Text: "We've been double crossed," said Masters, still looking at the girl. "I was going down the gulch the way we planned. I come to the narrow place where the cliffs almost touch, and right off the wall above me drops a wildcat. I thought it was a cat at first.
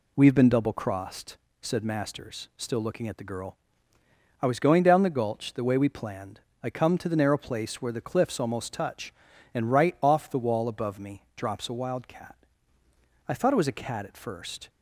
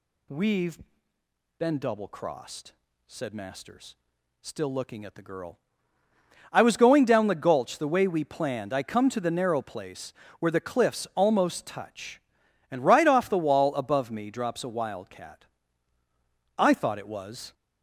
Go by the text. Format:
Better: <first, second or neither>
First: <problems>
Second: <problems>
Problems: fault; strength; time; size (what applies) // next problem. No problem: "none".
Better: first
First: none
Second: pauses between "We've" and "been"; noticeable; at 0.7 s; 0.80 s long // pauses between "place" and "where"; slight; at 10.1 s; 0.24 s long // stops before "a cat at first"; at 17.5 s